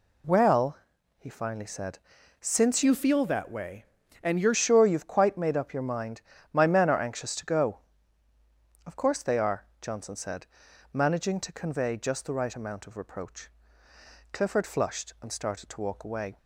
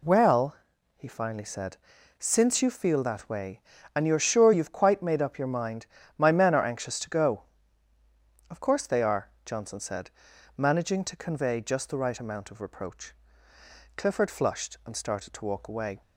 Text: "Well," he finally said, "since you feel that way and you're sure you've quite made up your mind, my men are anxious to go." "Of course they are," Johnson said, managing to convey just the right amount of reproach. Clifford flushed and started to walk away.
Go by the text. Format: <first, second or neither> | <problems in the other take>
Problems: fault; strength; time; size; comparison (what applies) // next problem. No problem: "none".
second | changes voice from "you" to "you're"; from 2.8 to 4.5 s; 1.7 s long